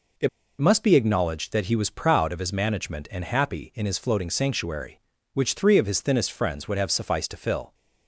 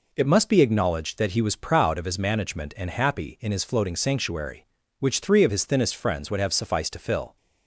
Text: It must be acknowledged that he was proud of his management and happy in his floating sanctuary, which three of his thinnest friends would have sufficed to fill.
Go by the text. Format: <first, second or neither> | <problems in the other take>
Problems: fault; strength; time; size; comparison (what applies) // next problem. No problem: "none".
second | pauses between "It" and "must"; slight; at 0.2 s; 0.30 s long